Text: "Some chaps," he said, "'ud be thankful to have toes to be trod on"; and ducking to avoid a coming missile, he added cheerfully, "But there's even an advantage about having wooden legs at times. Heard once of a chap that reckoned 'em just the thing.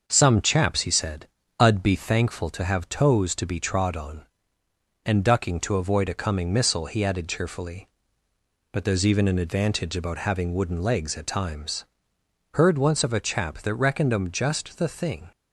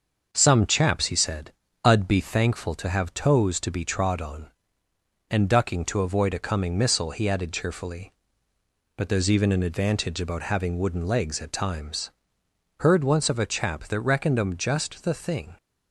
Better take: neither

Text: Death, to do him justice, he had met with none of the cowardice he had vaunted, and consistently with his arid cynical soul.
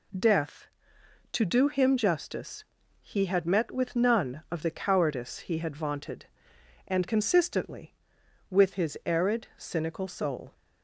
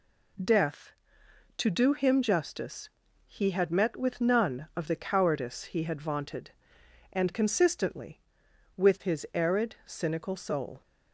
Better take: neither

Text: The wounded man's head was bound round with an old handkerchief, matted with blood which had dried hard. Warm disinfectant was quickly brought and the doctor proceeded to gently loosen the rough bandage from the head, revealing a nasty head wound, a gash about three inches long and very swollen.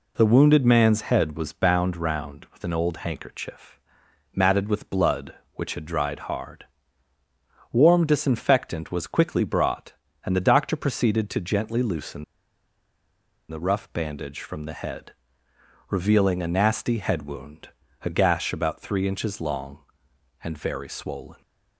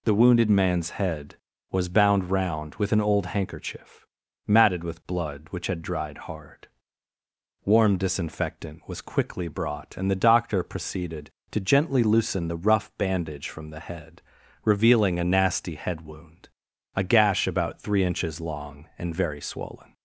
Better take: second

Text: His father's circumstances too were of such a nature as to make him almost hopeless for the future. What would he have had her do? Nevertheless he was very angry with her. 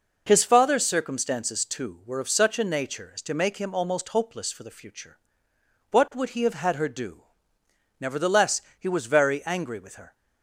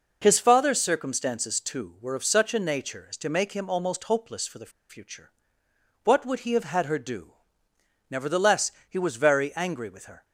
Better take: first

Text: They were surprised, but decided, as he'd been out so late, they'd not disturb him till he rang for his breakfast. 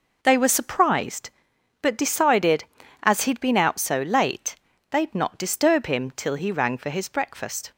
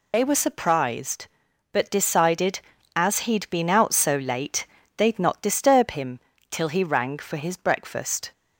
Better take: first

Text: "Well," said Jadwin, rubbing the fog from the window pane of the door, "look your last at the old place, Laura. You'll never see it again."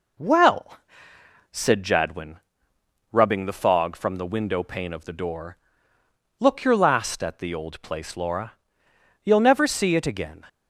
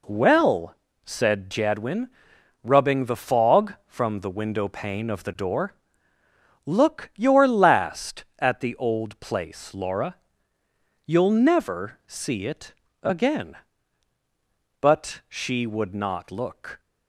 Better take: first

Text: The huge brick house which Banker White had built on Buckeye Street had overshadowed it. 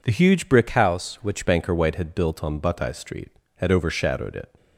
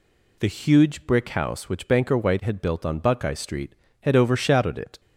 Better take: second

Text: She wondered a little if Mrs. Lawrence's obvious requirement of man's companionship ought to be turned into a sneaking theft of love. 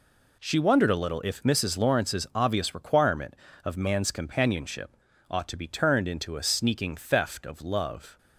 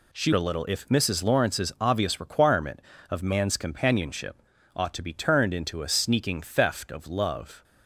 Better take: first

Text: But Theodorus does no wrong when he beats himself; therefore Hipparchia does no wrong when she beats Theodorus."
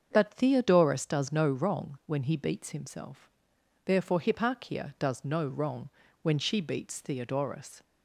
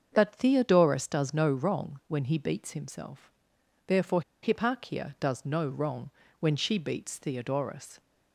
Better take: first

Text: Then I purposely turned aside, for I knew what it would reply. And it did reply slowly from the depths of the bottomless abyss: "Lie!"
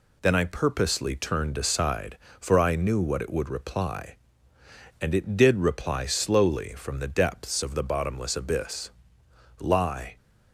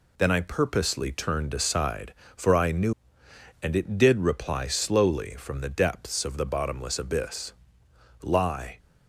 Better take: first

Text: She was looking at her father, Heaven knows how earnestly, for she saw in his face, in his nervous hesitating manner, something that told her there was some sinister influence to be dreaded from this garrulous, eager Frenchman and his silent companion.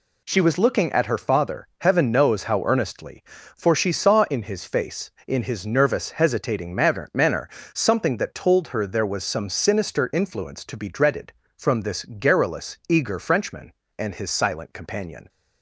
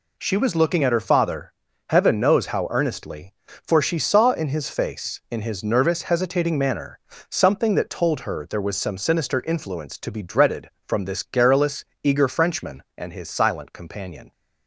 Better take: second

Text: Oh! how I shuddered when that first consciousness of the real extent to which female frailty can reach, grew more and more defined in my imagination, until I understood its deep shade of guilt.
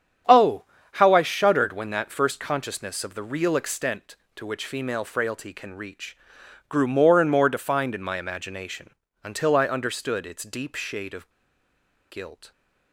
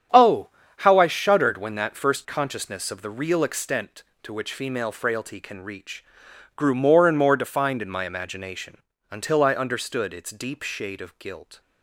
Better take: second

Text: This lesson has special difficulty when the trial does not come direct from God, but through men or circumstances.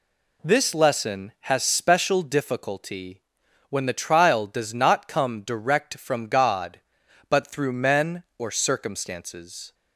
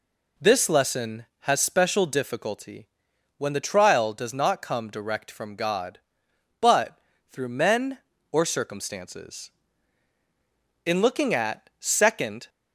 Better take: first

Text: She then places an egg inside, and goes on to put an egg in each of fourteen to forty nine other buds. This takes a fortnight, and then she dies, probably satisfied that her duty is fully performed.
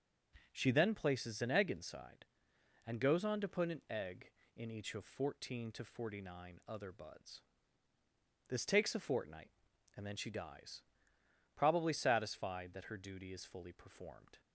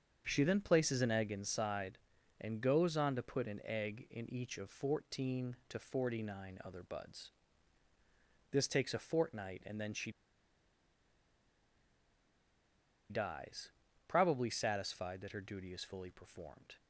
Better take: first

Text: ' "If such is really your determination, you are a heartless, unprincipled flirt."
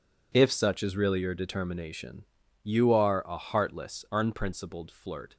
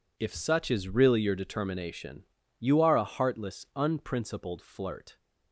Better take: neither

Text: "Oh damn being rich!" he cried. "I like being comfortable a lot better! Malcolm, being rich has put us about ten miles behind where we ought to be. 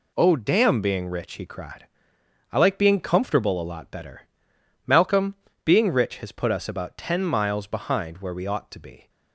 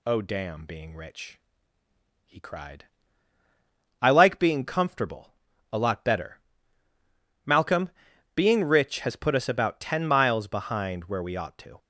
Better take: first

